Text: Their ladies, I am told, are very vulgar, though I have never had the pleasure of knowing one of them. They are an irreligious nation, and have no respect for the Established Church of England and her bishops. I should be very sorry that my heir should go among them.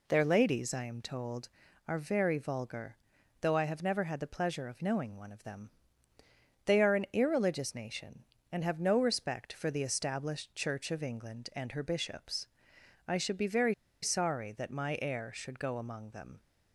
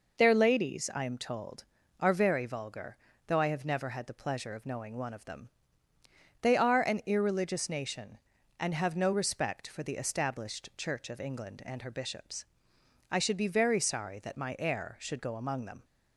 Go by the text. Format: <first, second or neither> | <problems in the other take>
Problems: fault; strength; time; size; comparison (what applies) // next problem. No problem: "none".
second | pauses between "very" and "sorry"; slight; at 13.7 s; 0.29 s long